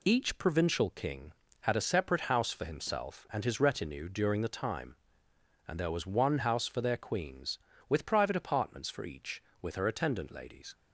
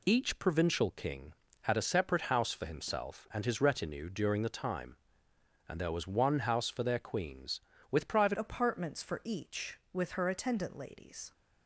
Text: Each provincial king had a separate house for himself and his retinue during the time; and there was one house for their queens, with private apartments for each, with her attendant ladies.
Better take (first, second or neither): first